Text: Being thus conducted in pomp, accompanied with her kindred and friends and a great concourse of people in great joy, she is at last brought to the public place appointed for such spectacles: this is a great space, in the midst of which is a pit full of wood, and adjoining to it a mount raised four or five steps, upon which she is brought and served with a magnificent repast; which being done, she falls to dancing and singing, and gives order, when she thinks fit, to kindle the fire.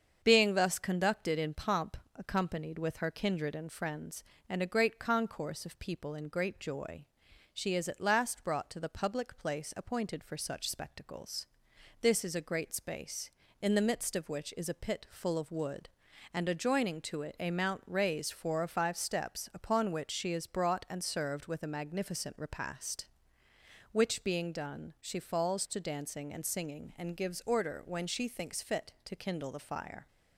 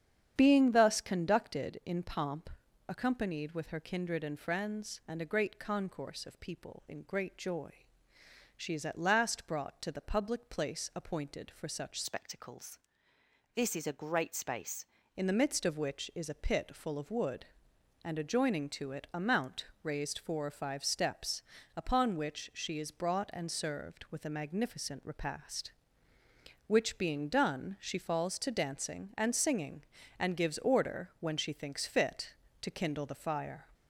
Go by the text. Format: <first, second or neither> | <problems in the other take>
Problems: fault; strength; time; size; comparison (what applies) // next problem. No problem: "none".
first | starts louder than the rest; strong; until 1.3 s; 8.5 dB; also in the first // changes voice from "spectacles" to "space"; from 12.0 to 14.8 s; 2.8 s long // pauses between "mount" and "raised"; slight; at 19.6 s; 0.16 s long